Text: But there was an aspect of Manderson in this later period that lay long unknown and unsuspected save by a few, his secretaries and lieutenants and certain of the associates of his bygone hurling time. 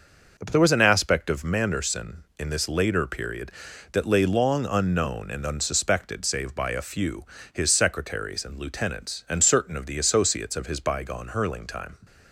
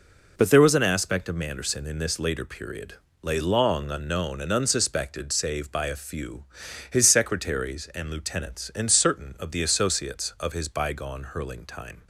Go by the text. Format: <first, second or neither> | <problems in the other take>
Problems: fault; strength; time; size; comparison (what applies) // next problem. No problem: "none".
first | skips "that"; at 3.0 s